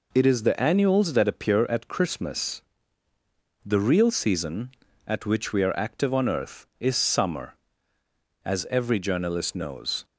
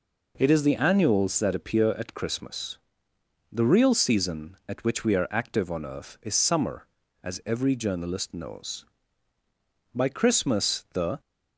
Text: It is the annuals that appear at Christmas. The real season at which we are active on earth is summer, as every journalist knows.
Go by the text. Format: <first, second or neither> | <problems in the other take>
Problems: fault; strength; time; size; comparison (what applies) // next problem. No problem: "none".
first | goes on to say "By Christmas the"; noticeable; from 9.9 s on; 1.2 s long